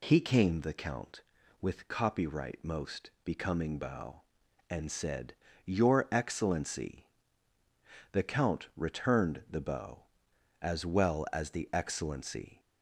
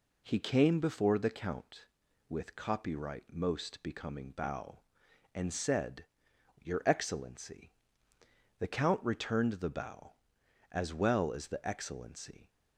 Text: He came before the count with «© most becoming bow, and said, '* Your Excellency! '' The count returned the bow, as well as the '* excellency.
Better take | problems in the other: second | skips "before"; at 0.5 s

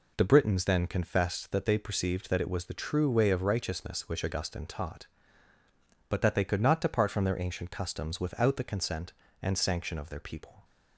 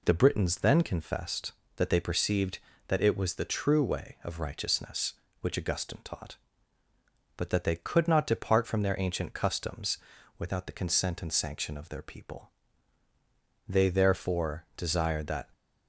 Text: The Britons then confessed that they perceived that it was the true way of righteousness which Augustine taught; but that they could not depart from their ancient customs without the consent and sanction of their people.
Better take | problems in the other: first | pauses between "customs" and "without"; at 9.9 s; 0.40 s long // goes on to say "They therefore desired that"; strong; from 13.6 s on; 1.8 s long

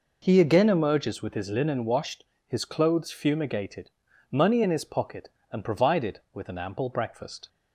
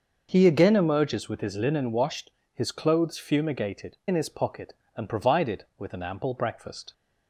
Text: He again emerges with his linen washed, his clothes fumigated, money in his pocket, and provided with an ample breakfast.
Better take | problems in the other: first | starts louder than the rest; until 1.3 s; 6 dB // skips "money"; at 4.0 s

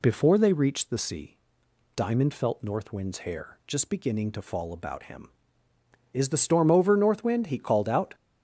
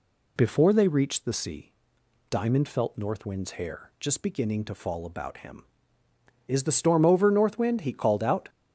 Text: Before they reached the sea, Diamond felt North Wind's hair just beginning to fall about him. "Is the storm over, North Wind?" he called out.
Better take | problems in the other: neither | none

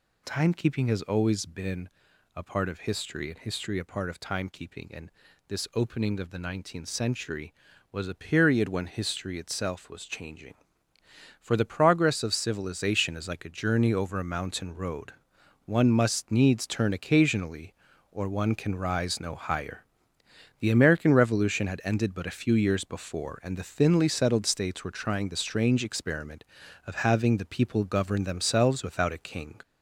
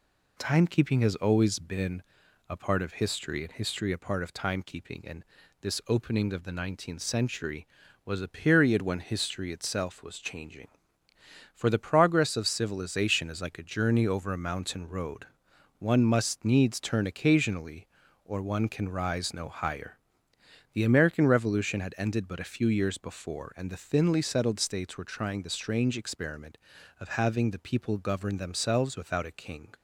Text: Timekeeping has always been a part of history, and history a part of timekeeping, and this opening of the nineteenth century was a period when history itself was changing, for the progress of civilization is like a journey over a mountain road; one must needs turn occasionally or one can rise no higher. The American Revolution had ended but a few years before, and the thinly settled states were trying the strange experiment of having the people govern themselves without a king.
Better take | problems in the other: second | gets louder; noticeable; throughout; 4 dB // pauses between "been" and "a"; noticeable; at 1.8 s; 0.46 s long; noticeable in the second // pauses between "and" and "this"; at 5.0 s; 0.38 s long; also in the second

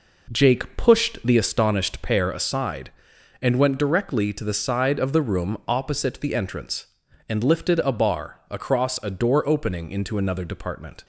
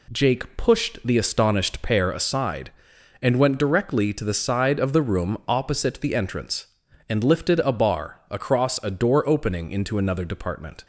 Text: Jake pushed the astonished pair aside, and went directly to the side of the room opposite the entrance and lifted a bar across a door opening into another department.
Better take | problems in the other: second | starts louder than the rest; noticeable; until 1.5 s; 4.5 dB

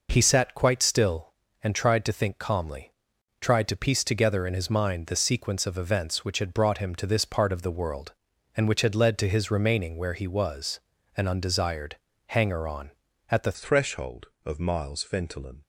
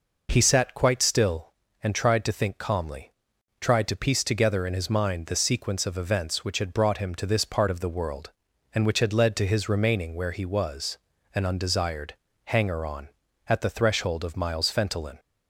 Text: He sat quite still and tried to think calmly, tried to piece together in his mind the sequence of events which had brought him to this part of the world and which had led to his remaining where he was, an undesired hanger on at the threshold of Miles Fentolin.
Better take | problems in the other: second | pauses between "undesired" and "hanger"; slight; at 11.9 s; 0.32 s long; slight in the second // changes voice at "threshold"; from 13.5 s on; 2.1 s long

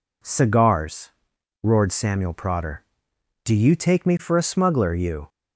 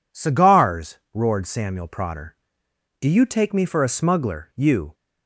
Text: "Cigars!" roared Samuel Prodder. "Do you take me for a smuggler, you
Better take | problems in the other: neither | none

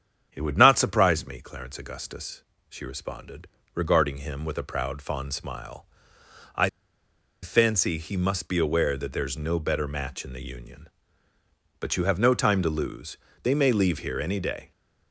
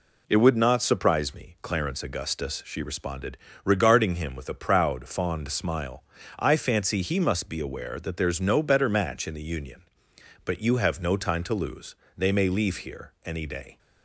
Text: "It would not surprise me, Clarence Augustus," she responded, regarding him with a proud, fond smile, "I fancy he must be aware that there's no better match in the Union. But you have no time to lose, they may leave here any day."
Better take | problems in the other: second | starts louder than the rest; strong; until 1.3 s; 8 dB // pauses between "I" and "fancy"; noticeable; at 6.6 s; 0.73 s long

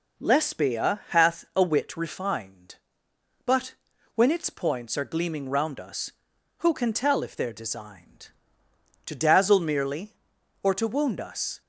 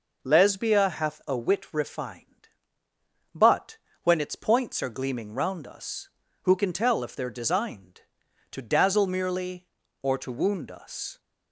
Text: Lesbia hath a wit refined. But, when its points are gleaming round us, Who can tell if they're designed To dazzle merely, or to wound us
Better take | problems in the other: neither | none

